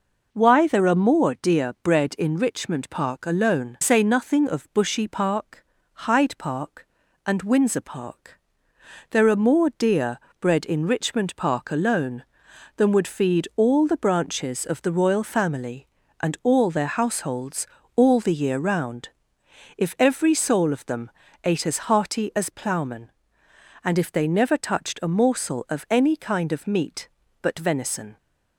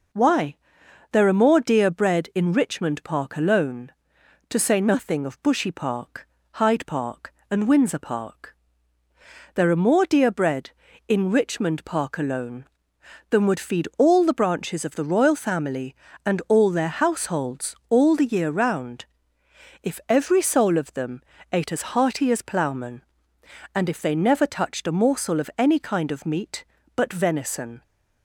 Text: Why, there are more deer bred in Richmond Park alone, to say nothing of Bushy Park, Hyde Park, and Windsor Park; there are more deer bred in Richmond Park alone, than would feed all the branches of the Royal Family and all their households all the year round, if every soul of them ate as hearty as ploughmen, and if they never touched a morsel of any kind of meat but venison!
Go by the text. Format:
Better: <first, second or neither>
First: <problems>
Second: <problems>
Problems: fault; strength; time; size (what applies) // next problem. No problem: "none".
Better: second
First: skips "to"; at 3.7 s // pauses between "deer" and "bred"; slight; at 10.1 s; 0.20 s long // pauses between "households" and "all"; slight; at 17.6 s; 0.30 s long // pauses between "them" and "ate"; slight; at 21.0 s; 0.34 s long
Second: pauses between "them" and "ate"; slight; at 21.2 s; 0.30 s long